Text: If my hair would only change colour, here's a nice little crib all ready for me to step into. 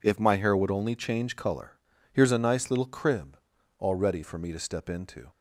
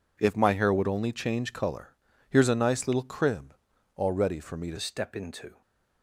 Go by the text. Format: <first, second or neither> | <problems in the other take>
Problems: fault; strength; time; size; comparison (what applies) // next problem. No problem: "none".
first | pauses between "crib" and "all"; at 3.5 s; 0.40 s long; also in the first // changes voice at "step"; from 4.7 s on; 0.9 s long // stays silent after the last word; slight; from 5.5 s on; 0.5 s long